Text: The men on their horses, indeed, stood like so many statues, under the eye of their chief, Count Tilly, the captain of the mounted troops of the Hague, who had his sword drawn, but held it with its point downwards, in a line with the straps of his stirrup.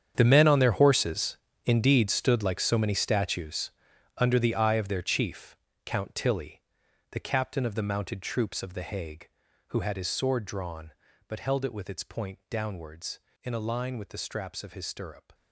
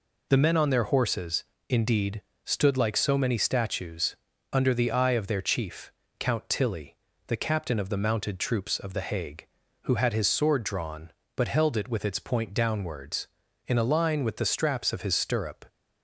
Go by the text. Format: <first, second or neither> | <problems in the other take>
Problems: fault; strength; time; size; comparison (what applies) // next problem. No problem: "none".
second | gets quieter; strong; throughout; 15 dB